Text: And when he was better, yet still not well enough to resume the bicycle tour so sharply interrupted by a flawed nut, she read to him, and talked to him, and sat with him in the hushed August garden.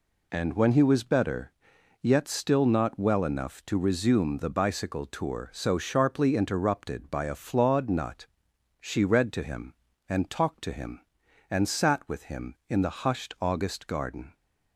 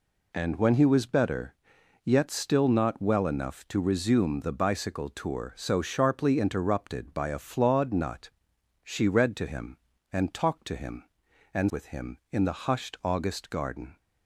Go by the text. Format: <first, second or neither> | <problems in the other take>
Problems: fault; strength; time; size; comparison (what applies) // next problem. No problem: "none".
first | skips "sat"; at 11.7 s